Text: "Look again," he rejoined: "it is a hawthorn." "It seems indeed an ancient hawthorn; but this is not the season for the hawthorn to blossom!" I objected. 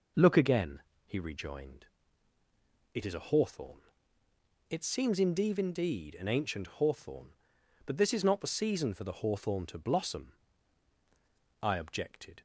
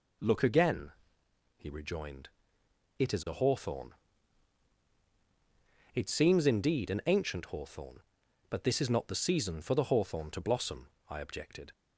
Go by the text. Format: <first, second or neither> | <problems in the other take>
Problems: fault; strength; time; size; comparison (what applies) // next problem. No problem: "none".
second | says "indeed" twice; at 5.5 s